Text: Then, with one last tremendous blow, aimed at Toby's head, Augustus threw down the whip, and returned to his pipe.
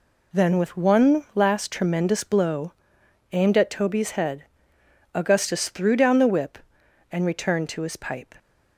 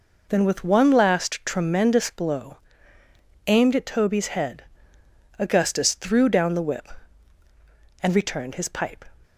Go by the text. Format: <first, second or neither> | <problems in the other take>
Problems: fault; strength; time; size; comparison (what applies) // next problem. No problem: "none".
first | skips "to"; at 8.5 s